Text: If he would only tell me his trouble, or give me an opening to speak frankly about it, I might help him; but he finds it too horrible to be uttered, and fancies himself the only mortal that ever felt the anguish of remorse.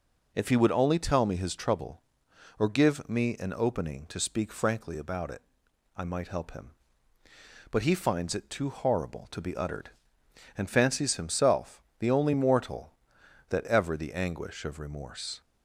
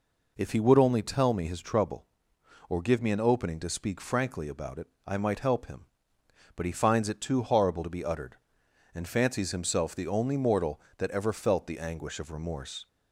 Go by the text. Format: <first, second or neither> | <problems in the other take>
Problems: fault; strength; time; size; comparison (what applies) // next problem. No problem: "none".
second | pauses between "himself" and "the"; slight; at 11.8 s; 0.16 s long // skips "felt"; at 13.9 s